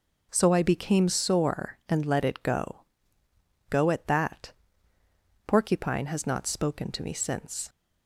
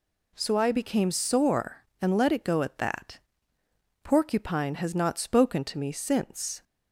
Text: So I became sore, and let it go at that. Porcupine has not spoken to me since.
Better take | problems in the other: second | says "go" twice; at 3.7 s

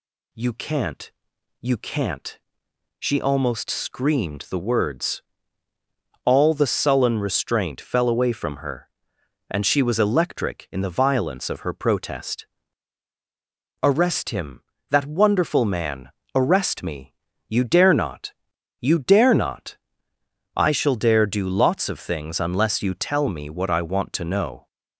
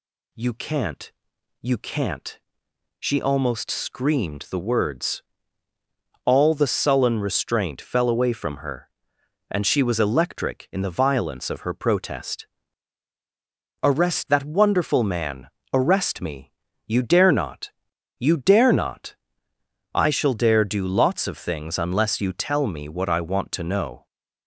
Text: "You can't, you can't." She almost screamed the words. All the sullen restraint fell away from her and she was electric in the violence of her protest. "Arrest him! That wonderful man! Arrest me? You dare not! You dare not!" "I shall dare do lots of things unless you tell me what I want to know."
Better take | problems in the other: first | skips "him"; at 14.2 s

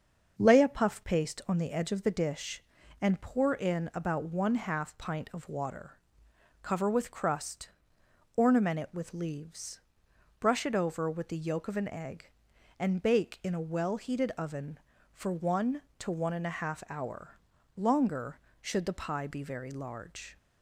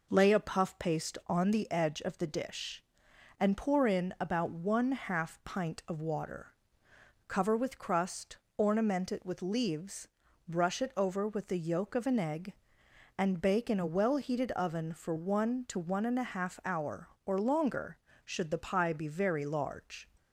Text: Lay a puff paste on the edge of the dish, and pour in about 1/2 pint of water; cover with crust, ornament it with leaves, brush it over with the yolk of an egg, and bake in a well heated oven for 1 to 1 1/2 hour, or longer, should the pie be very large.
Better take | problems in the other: second | starts louder than the rest; until 1.3 s; 6.5 dB // skips "or"; at 17.5 s

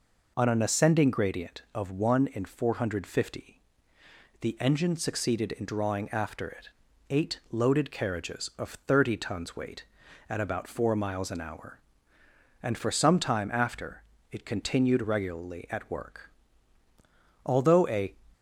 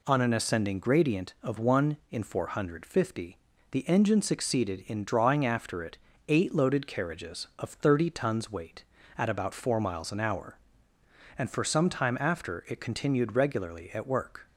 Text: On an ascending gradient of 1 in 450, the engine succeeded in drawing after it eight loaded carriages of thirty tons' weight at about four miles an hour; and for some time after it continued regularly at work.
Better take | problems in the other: second | pauses between "it" and "eight"; at 6.6 s; 0.42 s long; slight in the second // pauses between "after" and "it"; slight; at 14.0 s; 0.26 s long // goes on to say "Although a"; noticeable; from 17.4 s on; 0.70 s long

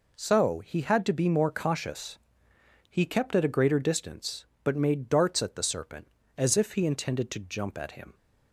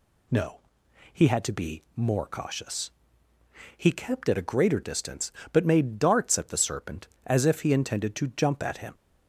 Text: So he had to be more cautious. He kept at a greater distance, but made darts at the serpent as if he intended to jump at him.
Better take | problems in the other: first | says "No" for "So"; at 0.2 s

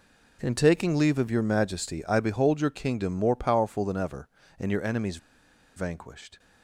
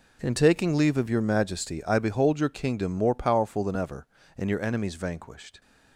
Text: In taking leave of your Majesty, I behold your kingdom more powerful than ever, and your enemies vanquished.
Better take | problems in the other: second | pauses between "enemies" and "vanquished"; noticeable; at 5.1 s; 0.58 s long

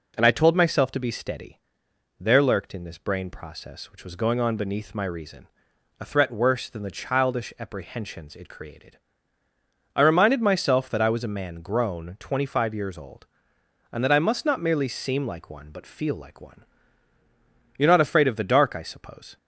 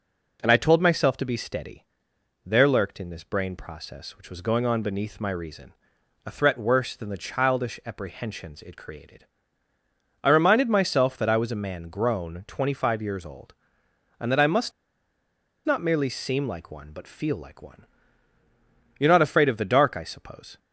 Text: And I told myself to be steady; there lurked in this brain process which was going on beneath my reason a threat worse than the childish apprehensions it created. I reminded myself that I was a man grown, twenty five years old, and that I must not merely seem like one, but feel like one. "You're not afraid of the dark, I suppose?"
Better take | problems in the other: first | pauses between "reason" and "a"; noticeable; at 5.7 s; 0.52 s long; noticeable in the first // pauses between "must" and "not"; noticeable; at 14.7 s; 0.94 s long

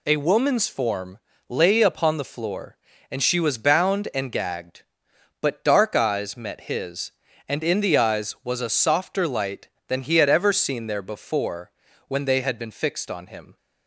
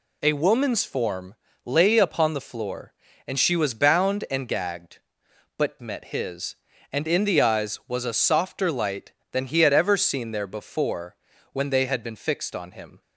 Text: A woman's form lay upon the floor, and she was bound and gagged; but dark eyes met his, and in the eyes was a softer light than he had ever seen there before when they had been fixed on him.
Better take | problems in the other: first | pauses between "form" and "lay"; slight; at 1.3 s; 0.28 s long; slight in the first // skips "dark eyes"; at 5.7 s // pauses between "before" and "when"; at 11.1 s; 0.38 s long; also in the first

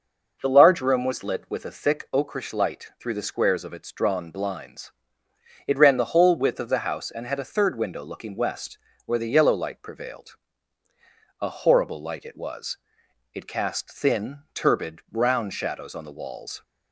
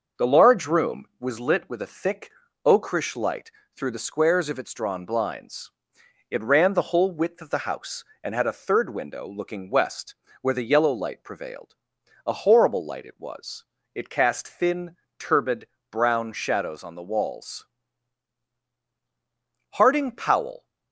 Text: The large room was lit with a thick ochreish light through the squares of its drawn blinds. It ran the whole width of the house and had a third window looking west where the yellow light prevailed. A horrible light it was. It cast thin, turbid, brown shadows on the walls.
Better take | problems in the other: first | starts louder than the rest; until 1.3 s; 6 dB // pauses between "thick" and "ochreish"; slight; at 2.3 s; 0.34 s long // pauses between "light" and "through"; slight; at 3.5 s; 0.24 s long // pauses between "west" and "where"; slight; at 10.1 s; 0.26 s long; slight in the first // goes on to say "Harding Powell"; noticeable; from 19.7 s on; 0.94 s long

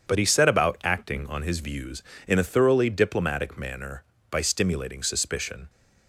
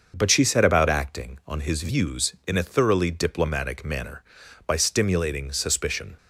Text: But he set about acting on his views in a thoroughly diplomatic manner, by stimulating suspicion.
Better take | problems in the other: first | starts louder than the rest; until 1.1 s; 6.5 dB; strong in the first // says "she" for "he"; at 0.3 s

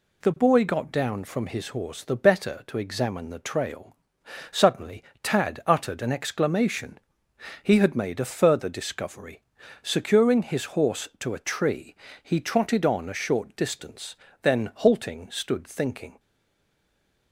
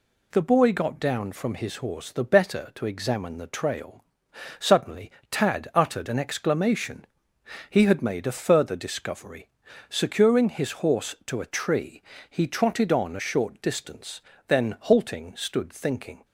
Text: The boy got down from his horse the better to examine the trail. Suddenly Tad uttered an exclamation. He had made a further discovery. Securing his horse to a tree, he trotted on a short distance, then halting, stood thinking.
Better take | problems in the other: second | pauses between "Suddenly" and "Tad"; slight; at 5.0 s; 0.18 s long; slight in the second // stays silent after the last word; noticeable; from 16.1 s on; 1.2 s long

